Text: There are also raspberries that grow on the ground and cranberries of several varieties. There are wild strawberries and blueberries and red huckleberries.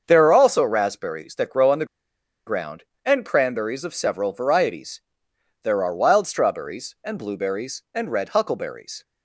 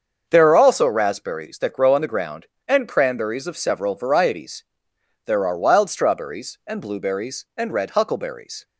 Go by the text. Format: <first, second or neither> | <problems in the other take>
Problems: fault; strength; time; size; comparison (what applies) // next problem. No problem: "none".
second | starts louder than the rest; until 1.0 s; 6.5 dB; also in the second // pauses between "the" and "ground"; noticeable; at 1.8 s; 0.61 s long